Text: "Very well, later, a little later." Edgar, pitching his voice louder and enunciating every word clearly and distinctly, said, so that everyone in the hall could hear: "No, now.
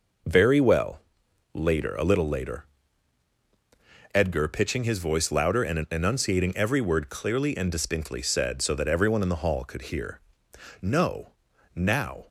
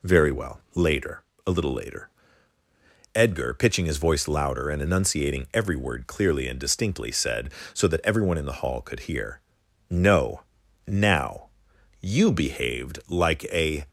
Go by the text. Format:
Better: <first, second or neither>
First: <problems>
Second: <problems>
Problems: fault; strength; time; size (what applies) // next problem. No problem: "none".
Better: first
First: none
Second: goes on to say "You behaved like a"; strong; from 12.1 s on; 1.7 s long